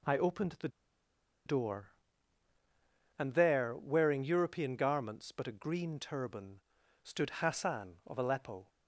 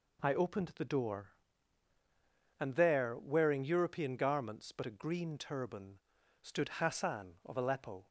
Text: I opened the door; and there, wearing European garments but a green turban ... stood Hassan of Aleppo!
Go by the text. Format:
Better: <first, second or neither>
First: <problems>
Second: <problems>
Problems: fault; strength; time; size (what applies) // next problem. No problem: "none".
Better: second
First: pauses between "the" and "door"; noticeable; at 0.6 s; 0.78 s long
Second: none